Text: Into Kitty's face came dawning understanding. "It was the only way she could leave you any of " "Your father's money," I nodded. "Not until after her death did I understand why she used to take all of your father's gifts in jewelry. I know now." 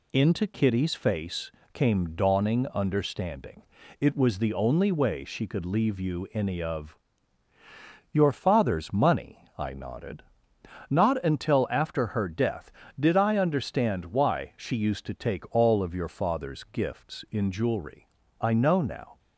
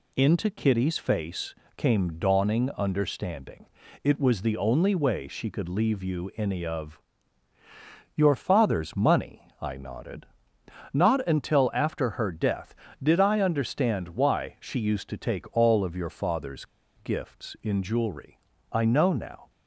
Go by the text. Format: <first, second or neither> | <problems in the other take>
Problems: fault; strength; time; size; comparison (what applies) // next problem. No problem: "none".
first | pauses between "face" and "came"; slight; at 1.5 s; 0.22 s long; slight in the first // pauses between "father's" and "gifts"; slight; at 16.6 s; 0.31 s long